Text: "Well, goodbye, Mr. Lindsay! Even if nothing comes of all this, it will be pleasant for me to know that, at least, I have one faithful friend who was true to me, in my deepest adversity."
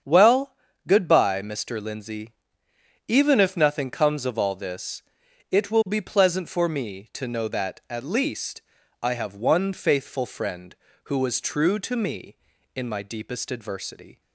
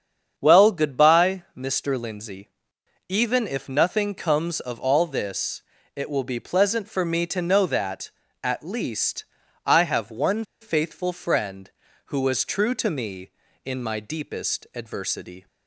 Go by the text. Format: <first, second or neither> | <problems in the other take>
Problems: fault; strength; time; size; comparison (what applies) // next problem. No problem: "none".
first | starts louder than the rest; strong; until 1.3 s; 7.5 dB; strong in the first // pauses between "one" and "faithful"; slight; at 10.4 s; 0.16 s long